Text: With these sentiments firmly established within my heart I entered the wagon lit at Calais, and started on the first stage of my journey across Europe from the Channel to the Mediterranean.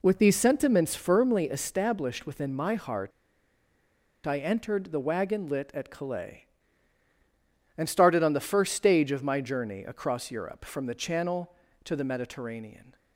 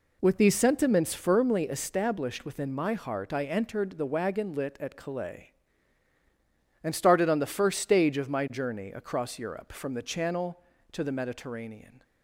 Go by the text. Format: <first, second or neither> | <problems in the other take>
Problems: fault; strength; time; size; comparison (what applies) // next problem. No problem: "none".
second | pauses between "heart" and "I"; at 3.1 s; 1.1 s long